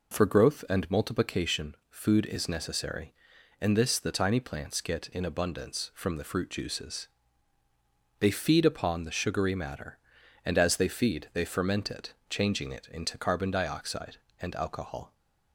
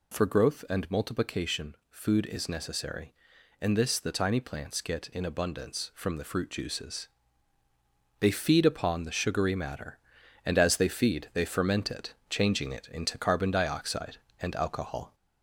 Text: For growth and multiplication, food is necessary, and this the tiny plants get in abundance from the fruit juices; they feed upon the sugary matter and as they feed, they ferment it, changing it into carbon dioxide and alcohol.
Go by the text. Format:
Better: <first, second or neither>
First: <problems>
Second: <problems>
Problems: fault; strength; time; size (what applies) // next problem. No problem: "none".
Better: first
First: none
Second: gets louder; slight; throughout; 3 dB